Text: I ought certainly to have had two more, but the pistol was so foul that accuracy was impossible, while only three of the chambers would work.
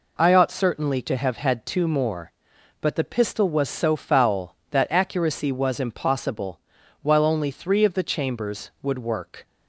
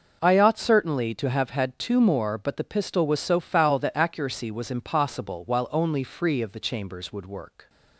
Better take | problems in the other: first | says "free" for "three"; at 6.0 s

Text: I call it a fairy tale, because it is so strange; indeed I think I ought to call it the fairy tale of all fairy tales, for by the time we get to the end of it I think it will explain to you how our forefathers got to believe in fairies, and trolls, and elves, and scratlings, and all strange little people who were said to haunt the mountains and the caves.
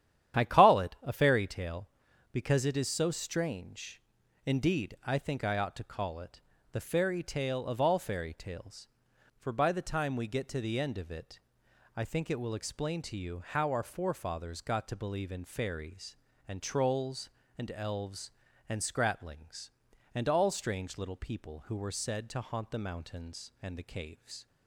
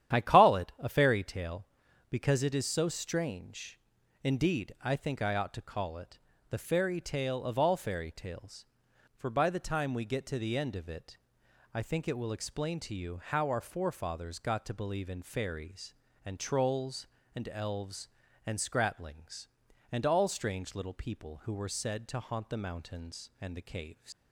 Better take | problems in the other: first | starts louder than the rest; strong; until 1.1 s; 10.5 dB; strong in the first // pauses between "it" and "the"; slight; at 6.1 s; 0.32 s long; slight in the first // pauses between "it" and "I"; noticeable; at 11.1 s; 0.58 s long; noticeable in the first // leaves "caves" unfinished; at 24.1 s; 125 ms

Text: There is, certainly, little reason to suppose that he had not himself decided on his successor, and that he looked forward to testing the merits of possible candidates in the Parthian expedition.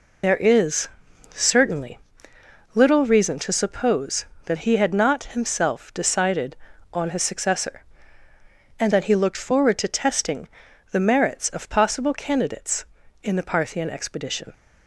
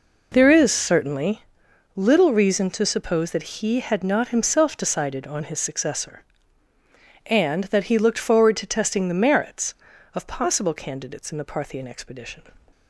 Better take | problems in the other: second | loses the start of "There"; at 0.2 s; 85 ms // pauses between "testing" and "the"; at 10.4 s; 0.44 s long

